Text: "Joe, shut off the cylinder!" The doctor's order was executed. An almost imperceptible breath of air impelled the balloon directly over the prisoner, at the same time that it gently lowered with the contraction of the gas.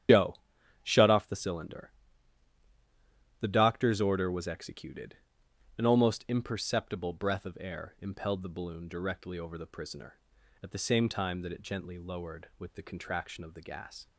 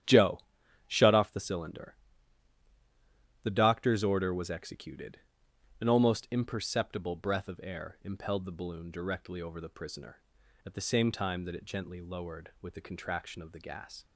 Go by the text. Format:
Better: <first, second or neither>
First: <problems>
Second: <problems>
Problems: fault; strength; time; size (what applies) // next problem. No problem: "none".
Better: second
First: loses the start of "Joe"; at 0.0 s; 85 ms // starts louder than the rest; strong; until 1.5 s; 9.5 dB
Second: starts louder than the rest; strong; until 1.5 s; 10 dB